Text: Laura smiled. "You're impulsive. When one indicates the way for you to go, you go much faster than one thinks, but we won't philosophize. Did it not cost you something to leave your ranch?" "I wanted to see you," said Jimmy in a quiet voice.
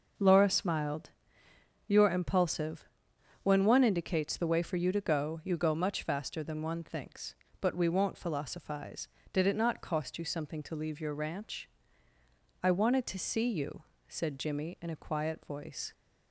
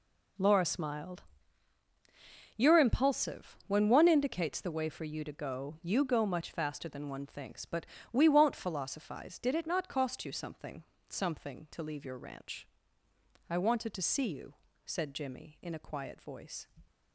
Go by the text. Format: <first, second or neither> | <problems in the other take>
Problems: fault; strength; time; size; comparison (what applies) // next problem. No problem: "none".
first | pauses between "but" and "we"; slight; at 7.8 s; 0.26 s long // says "something" twice; at 11.0 s